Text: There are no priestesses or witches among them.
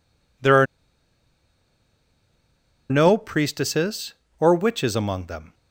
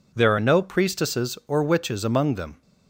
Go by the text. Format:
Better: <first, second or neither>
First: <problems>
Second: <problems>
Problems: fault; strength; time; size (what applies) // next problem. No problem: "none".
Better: second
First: pauses between "are" and "no"; strong; at 0.6 s; 2.2 s long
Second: none